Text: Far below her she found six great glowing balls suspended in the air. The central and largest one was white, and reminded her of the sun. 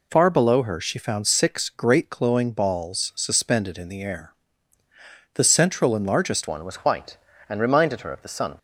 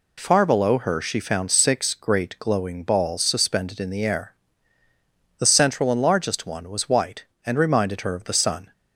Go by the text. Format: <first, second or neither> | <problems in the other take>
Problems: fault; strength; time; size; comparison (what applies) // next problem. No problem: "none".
second | changes voice at "one"; from 6.4 s on; 2.1 s long